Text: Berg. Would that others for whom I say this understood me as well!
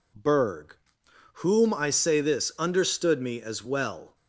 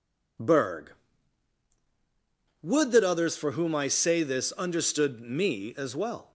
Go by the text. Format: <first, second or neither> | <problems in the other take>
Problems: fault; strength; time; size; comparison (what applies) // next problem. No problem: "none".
second | skips "Would that others for"; at 1.0 s